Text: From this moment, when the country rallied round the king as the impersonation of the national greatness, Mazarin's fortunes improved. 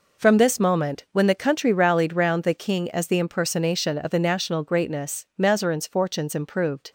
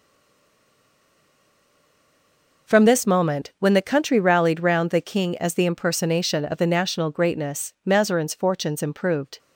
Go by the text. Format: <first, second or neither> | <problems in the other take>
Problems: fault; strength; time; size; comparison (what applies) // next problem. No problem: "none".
first | stays silent before the first word; strong; until 2.6 s; 2.6 s long